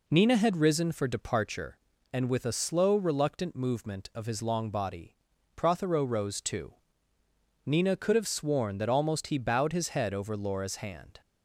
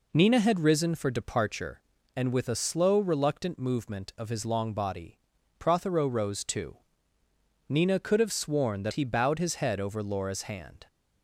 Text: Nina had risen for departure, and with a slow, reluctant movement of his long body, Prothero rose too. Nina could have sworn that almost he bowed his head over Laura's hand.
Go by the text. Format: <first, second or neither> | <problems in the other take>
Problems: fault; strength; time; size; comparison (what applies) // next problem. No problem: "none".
first | skips "almost"; at 8.9 s